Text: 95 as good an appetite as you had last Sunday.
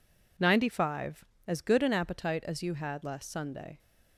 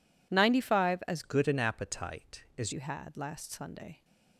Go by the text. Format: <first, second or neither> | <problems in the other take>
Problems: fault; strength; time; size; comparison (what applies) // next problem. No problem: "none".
first | changes voice from "good" to "as"; from 1.2 to 2.7 s; 1.5 s long